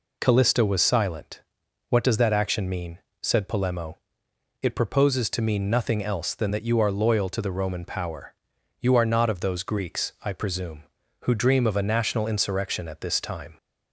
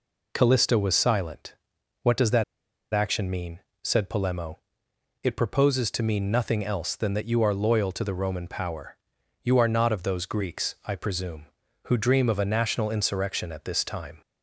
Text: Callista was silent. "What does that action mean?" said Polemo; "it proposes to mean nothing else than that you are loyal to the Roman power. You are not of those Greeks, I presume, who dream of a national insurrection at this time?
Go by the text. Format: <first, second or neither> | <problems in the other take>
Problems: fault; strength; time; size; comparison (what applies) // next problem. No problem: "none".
first | pauses between "that" and "action"; noticeable; at 2.4 s; 0.48 s long